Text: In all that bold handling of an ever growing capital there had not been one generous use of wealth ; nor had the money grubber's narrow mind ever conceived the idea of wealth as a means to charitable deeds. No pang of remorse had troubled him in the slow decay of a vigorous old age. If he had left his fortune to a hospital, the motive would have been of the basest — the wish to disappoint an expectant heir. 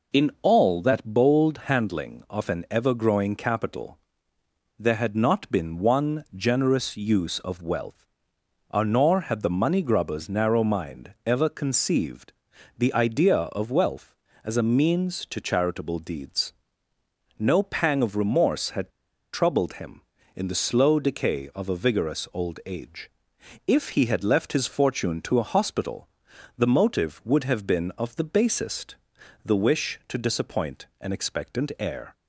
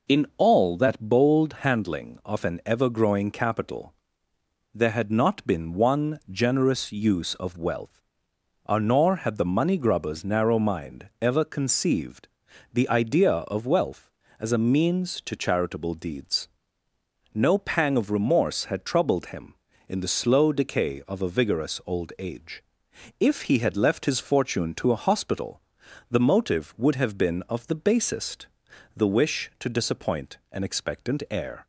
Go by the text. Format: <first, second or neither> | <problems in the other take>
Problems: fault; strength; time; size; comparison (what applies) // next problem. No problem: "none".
second | pauses between "capital" and "there"; noticeable; at 3.9 s; 0.80 s long; noticeable in the second // pauses between "conceived" and "the"; at 12.3 s; 0.44 s long; also in the second // pauses between "had" and "troubled"; at 18.8 s; 0.43 s long